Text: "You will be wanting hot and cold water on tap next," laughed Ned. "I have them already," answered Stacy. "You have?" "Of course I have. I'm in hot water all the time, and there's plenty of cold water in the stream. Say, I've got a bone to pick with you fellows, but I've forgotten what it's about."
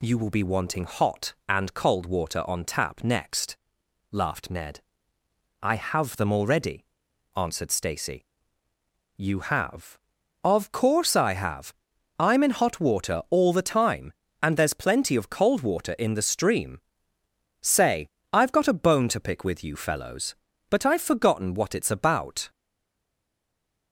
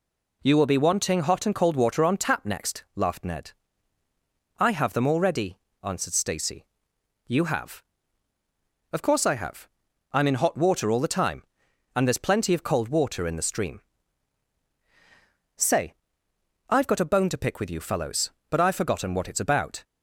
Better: second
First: stays silent after the last word; noticeable; from 22.4 s on; 1.5 s long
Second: none

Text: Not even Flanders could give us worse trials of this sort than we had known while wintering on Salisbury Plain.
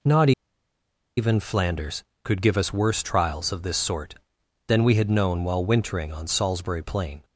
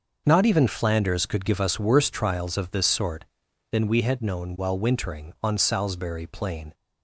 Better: second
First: pauses between "Not" and "even"; noticeable; at 0.3 s; 0.86 s long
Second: none

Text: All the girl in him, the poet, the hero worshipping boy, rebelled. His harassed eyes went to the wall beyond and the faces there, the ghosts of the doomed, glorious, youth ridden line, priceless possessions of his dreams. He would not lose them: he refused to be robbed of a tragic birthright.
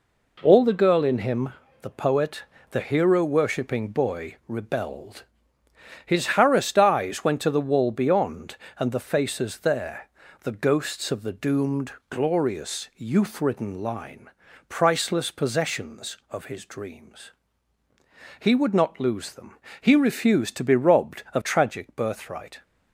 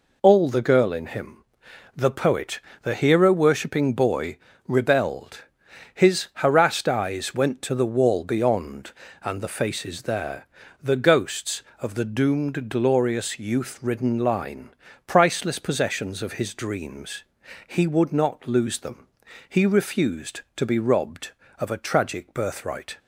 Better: second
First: skips "a"; at 21.4 s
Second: none

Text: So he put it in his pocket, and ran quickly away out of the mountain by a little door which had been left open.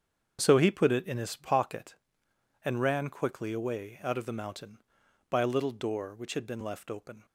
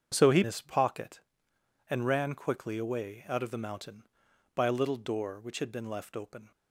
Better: first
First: starts louder than the rest; strong; until 1.4 s; 7.5 dB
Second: starts louder than the rest; strong; until 1.1 s; 7.5 dB // skips "put it in"; at 0.4 s

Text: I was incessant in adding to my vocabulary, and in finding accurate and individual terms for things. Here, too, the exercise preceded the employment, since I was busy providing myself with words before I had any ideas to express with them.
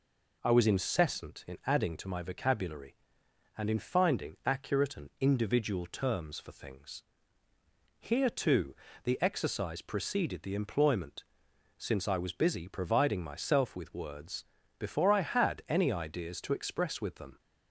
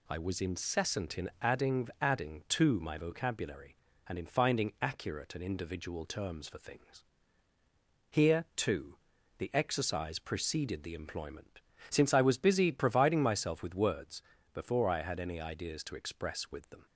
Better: first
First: pauses between "words" and "before"; slight; at 14.4 s; 0.34 s long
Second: says "adding" twice; at 1.9 s // pauses between "words" and "before"; slight; at 14.2 s; 0.32 s long

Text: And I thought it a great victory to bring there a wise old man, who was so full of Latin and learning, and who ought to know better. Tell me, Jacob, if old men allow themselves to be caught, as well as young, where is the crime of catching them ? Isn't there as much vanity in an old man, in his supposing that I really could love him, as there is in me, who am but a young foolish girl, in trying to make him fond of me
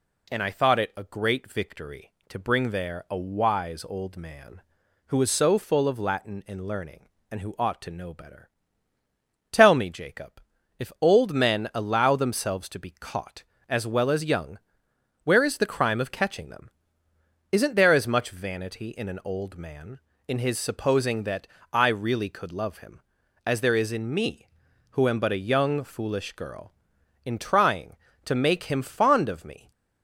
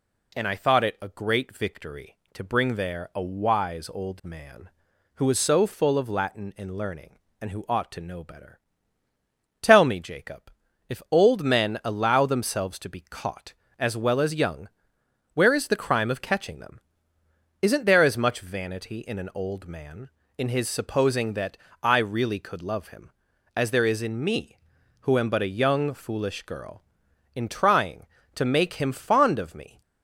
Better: neither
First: pauses between "that" and "I"; slight; at 21.4 s; 0.26 s long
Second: pauses between "that" and "I"; slight; at 21.5 s; 0.26 s long

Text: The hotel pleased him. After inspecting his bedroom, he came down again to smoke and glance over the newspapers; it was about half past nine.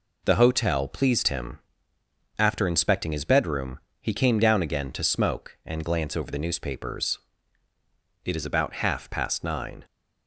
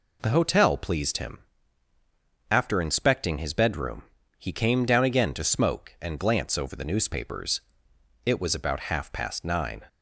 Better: second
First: says "is" for "was"; at 8.3 s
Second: none

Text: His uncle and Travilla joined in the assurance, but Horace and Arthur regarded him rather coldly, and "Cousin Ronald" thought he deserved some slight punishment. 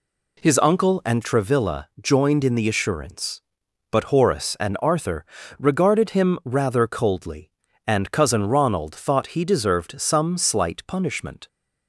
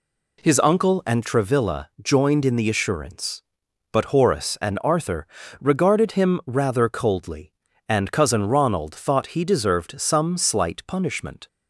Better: neither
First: pauses between "Arthur" and "regarded"; slight; at 5.2 s; 0.32 s long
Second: pauses between "Arthur" and "regarded"; slight; at 5.2 s; 0.32 s long

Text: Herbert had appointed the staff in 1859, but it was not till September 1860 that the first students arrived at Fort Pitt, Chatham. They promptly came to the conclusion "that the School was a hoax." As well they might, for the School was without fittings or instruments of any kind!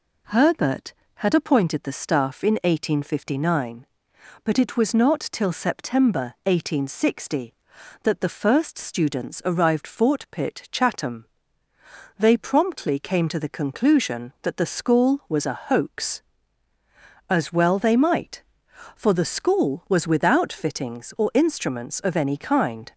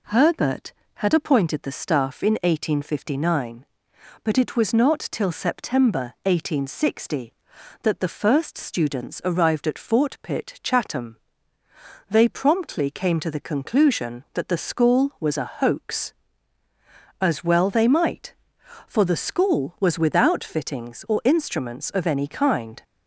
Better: second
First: skips "at"; at 9.8 s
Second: none

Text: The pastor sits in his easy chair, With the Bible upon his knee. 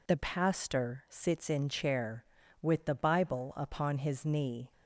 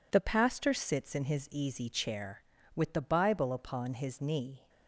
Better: second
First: skips "his easy"; at 1.6 s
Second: none

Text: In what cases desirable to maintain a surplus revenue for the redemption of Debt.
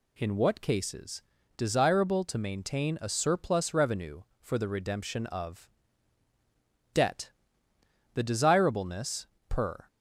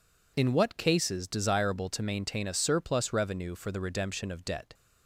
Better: second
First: pauses between "cases" and "desirable"; slight; at 1.2 s; 0.36 s long // pauses between "of" and "Debt"; at 5.6 s; 1.2 s long // goes on to say "The desirableness per"; strong; from 8.1 s on; 1.7 s long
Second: none

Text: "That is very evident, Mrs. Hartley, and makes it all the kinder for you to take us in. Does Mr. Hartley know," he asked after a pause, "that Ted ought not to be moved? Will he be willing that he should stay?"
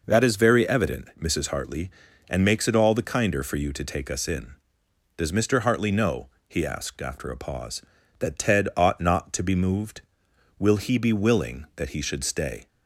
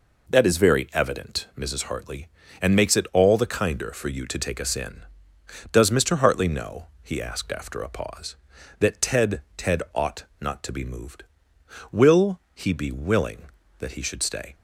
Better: first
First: none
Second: says "Ted" twice; at 9.5 s // pauses between "ought" and "not"; slight; at 10.2 s; 0.16 s long

